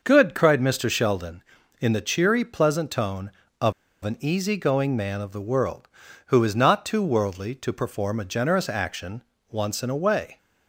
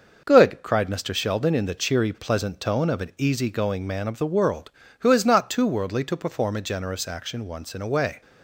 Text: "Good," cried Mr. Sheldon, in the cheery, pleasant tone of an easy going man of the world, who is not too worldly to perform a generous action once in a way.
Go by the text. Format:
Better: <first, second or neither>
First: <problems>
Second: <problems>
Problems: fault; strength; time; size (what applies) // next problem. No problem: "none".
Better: second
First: starts louder than the rest; noticeable; until 1.0 s; 6 dB // pauses between "of" and "an"; slight; at 3.7 s; 0.32 s long // pauses between "action" and "once"; slight; at 9.2 s; 0.28 s long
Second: starts louder than the rest; noticeable; until 1.2 s; 6 dB